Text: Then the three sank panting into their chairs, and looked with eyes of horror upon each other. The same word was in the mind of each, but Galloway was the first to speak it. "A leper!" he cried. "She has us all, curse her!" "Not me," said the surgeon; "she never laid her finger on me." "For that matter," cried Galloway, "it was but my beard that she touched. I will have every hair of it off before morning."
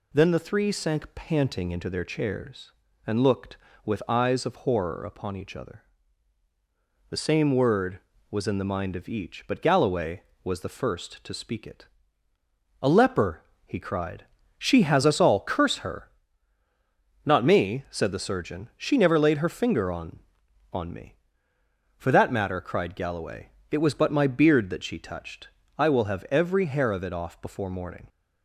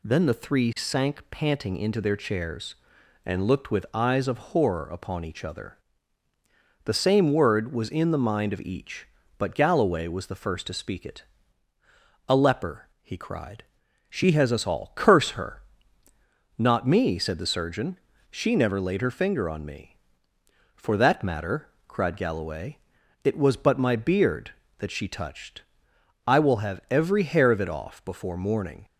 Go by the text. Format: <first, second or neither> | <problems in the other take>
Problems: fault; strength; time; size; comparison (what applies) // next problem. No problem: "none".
second | says "on" twice; at 20.7 s